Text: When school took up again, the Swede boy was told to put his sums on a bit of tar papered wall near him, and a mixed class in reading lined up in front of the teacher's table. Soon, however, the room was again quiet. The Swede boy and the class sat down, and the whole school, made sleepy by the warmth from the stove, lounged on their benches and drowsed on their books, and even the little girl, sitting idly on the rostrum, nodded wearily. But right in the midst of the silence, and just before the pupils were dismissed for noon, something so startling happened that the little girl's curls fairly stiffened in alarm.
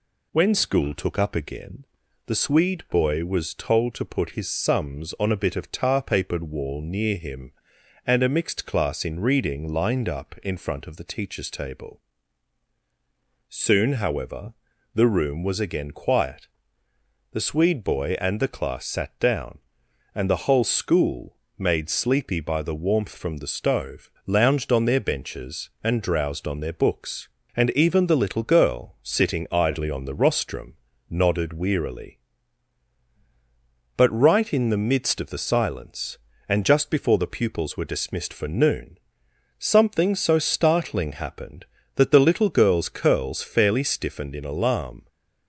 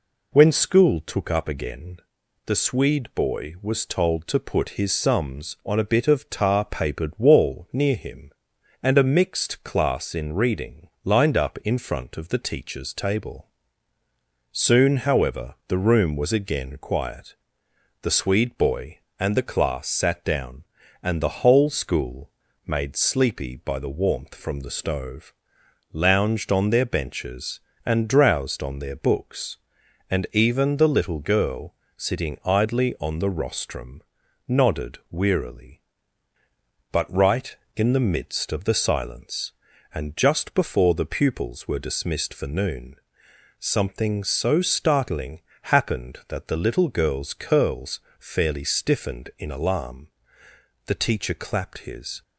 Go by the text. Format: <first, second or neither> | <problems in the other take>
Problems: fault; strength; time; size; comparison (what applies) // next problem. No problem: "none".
first | pauses between "reading" and "lined"; slight; at 10.8 s; 0.16 s long // pauses between "startling" and "happened"; slight; at 45.3 s; 0.22 s long // pauses between "curls" and "fairly"; slight; at 47.9 s; 0.20 s long // goes on to say "The teacher clapped his"; from 50.8 s on; 1.3 s long